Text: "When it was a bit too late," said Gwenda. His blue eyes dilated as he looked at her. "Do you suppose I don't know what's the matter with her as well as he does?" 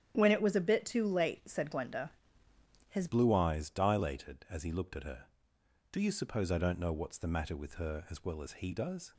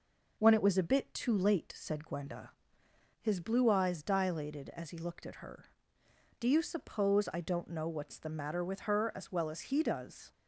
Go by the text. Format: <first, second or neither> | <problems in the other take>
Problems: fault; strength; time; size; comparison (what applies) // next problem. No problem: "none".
second | starts louder than the rest; strong; until 1.1 s; 10 dB // changes voice at "blue"; from 3.0 s on; 6.1 s long